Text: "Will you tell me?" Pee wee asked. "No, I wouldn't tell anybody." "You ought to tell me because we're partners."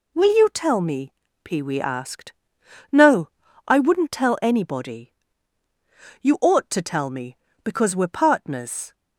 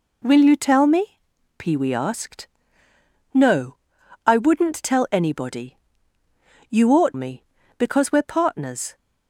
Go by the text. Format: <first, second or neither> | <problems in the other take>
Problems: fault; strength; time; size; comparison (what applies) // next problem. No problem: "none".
first | skips "to tell"; at 7.1 s